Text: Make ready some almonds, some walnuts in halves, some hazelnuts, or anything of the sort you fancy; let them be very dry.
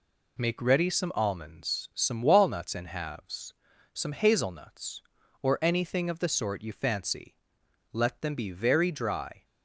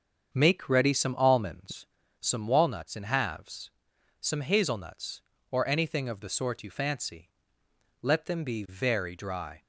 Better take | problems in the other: first | starts louder than the rest; until 1.9 s; 7 dB

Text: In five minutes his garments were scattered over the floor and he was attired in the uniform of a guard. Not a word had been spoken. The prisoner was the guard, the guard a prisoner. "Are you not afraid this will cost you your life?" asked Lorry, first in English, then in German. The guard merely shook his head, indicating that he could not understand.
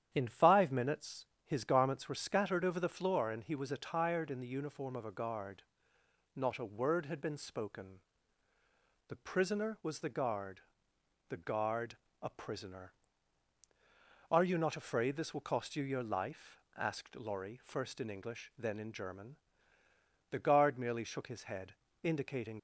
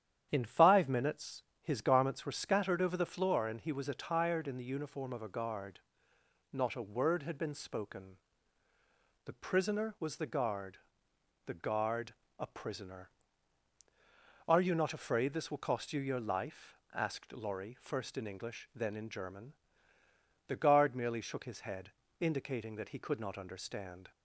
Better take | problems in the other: second | starts louder than the rest; strong; until 1.1 s; 10 dB; strong in the second // pauses between "minutes" and "his"; slight; at 1.2 s; 0.20 s long; slight in the second // pauses between "guard" and "a"; slight; at 11.9 s; 0.26 s long; slight in the second // stops before "that he could not understand"; at 22.5 s

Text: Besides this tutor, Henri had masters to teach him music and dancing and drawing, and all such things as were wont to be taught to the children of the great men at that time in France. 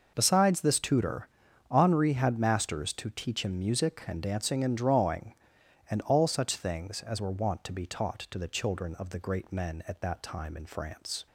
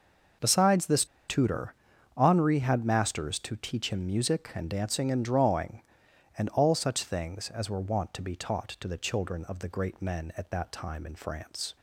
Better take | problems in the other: first | pauses between "this" and "tutor"; slight; at 1.0 s; 0.23 s long

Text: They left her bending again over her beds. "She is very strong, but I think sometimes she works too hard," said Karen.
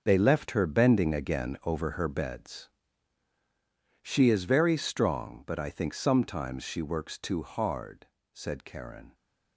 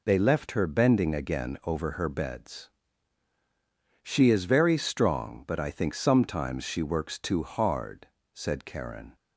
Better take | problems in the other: second | gets quieter; strong; throughout; 12 dB

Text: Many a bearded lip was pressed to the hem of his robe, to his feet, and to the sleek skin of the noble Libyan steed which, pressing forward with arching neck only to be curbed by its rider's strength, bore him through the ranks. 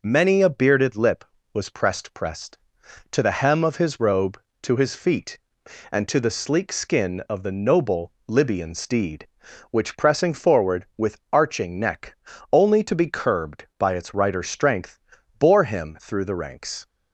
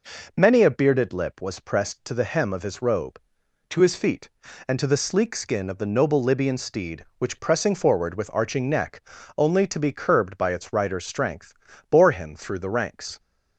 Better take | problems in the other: second | says "pressed" twice; at 2.1 s // pauses between "noble" and "Libyan"; slight; at 8.1 s; 0.16 s long // pauses between "neck" and "only"; slight; at 12.1 s; 0.36 s long; slight in the second

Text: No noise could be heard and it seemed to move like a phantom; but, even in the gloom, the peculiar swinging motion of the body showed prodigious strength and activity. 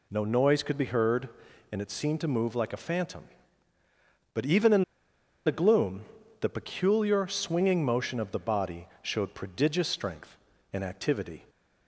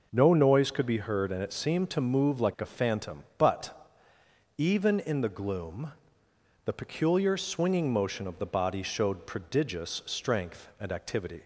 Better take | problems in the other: second | pauses between "in" and "the"; noticeable; at 4.8 s; 0.62 s long

